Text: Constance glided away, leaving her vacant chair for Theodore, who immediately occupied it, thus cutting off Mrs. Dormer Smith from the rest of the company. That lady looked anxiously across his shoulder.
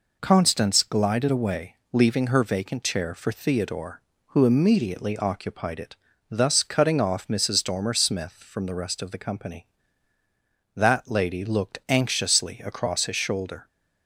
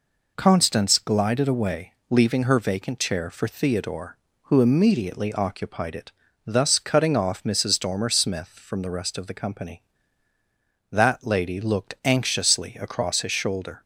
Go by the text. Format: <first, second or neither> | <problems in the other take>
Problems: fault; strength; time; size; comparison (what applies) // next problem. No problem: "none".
neither | none